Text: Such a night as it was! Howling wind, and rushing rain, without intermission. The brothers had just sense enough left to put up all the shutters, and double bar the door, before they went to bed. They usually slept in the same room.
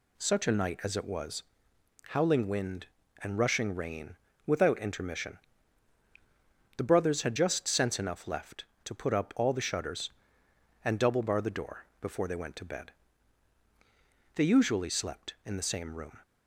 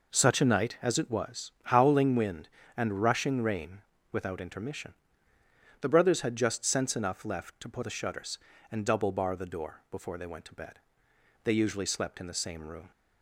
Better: first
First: none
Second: skips "up all"; at 7.8 s

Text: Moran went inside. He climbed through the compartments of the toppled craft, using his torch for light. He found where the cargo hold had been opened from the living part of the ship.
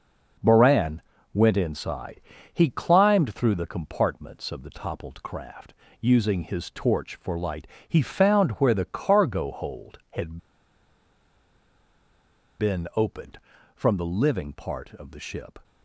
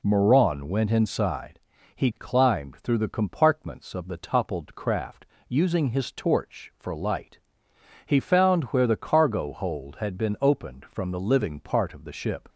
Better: second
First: pauses between "Moran" and "went"; slight; at 1.0 s; 0.32 s long // pauses between "had" and "been"; strong; at 10.3 s; 2.2 s long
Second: none

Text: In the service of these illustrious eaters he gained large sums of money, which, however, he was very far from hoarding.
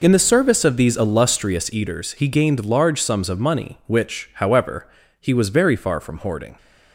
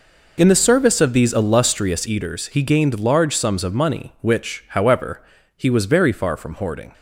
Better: neither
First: none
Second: none

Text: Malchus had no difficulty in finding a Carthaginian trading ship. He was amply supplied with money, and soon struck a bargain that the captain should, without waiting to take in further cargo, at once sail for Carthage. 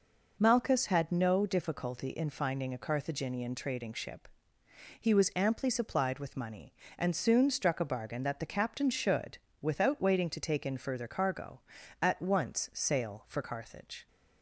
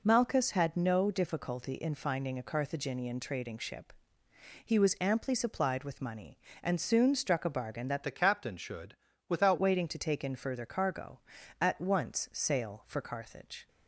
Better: first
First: none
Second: changes voice from "the" to "without"; from 8.0 to 9.5 s; 1.5 s long

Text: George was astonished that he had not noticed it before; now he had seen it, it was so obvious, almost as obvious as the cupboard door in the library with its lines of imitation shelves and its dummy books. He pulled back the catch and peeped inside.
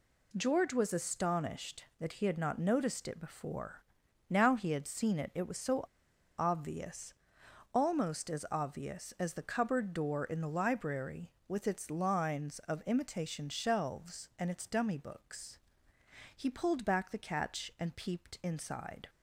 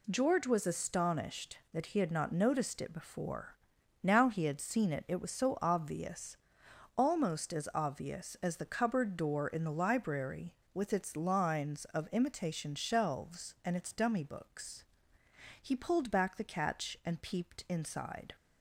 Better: second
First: pauses between "so" and "obvious"; noticeable; at 5.8 s; 0.56 s long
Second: none

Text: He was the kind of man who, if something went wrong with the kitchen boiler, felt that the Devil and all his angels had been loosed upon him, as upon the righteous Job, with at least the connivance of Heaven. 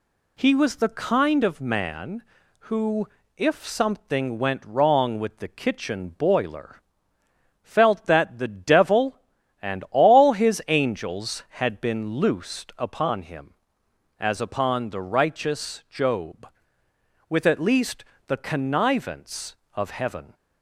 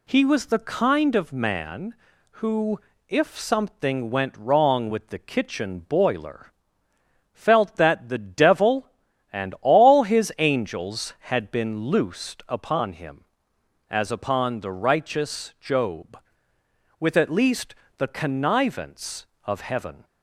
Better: neither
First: pauses between "least" and "the"; slight; at 18.0 s; 0.22 s long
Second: pauses between "least" and "the"; slight; at 17.7 s; 0.22 s long

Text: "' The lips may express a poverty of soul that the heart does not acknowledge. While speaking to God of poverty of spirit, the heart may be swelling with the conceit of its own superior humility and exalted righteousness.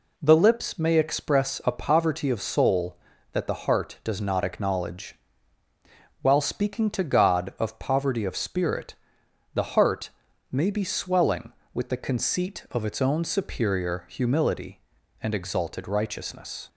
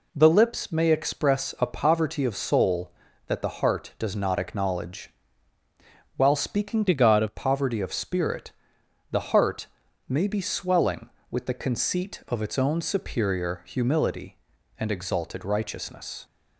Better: first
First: pauses between "heart" and "may"; at 10.1 s; 0.42 s long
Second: changes voice from "to" to "of"; from 6.8 to 7.3 s; 0.5 s long // pauses between "heart" and "may"; at 9.6 s; 0.42 s long

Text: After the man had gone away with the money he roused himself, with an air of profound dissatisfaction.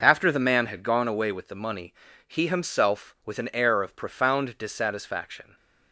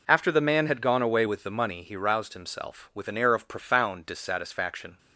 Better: second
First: pauses between "money" and "he"; slight; at 1.9 s; 0.34 s long // skips "roused"; at 2.4 s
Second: none

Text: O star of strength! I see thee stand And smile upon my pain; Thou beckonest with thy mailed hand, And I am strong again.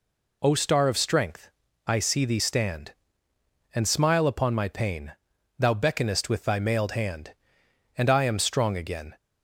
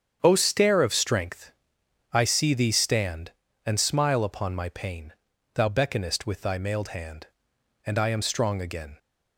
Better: first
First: none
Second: starts louder than the rest; strong; until 1.2 s; 8 dB // says "stair" for "star"; at 0.3 s

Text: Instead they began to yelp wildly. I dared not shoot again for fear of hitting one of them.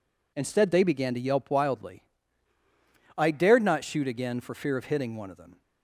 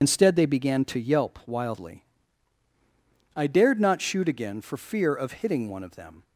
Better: first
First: none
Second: loses the start of "Instead"; at 0.0 s; 35 ms

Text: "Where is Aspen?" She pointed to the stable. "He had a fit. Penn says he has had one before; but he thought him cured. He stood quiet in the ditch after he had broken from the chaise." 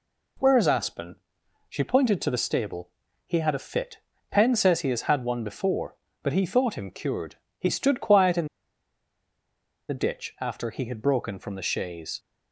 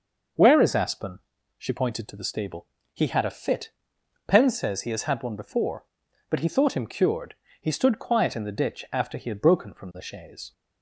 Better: second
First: pauses between "in" and "the"; strong; at 8.4 s; 1.4 s long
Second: none

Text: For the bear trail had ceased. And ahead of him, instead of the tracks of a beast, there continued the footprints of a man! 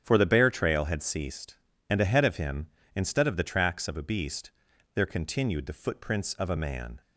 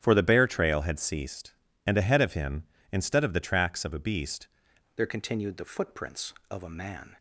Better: first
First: starts louder than the rest; strong; until 1.0 s; 9.5 dB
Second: starts louder than the rest; strong; until 1.0 s; 11 dB // changes voice at "there"; from 4.9 s on; 2.2 s long

